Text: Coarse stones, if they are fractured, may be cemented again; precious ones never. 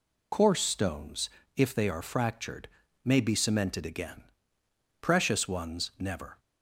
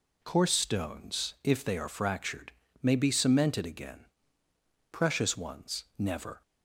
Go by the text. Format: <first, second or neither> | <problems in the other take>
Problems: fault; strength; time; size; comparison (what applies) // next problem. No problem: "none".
second | loses the start of "Coarse"; at 0.3 s; 40 ms